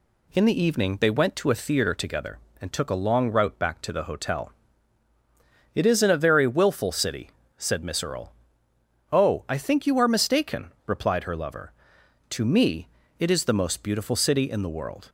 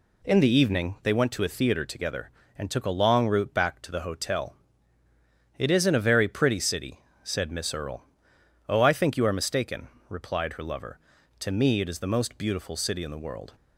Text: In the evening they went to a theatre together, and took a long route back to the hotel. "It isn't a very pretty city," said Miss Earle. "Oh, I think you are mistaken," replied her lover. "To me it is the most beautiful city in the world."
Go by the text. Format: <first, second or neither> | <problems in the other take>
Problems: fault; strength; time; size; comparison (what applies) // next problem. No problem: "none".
second | says "willful" for "pretty"; at 6.4 s // pauses between "me" and "it"; slight; at 12.8 s; 0.28 s long